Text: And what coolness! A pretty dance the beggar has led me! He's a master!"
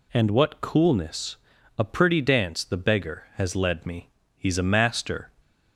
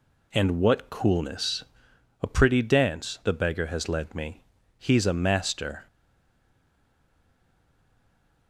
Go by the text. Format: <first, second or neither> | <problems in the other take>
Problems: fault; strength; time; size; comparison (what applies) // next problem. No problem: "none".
first | stays silent after the last word; strong; from 5.8 s on; 2.6 s long